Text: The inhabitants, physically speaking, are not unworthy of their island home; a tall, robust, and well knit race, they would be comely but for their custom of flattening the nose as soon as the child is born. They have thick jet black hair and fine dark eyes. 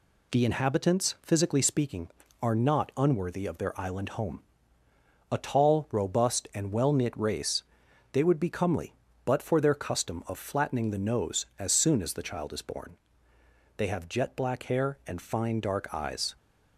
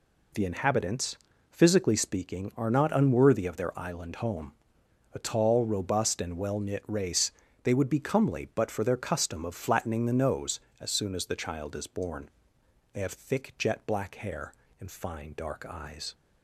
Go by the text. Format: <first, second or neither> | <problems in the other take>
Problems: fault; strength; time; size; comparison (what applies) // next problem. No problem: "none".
second | skips "thick"; at 14.0 s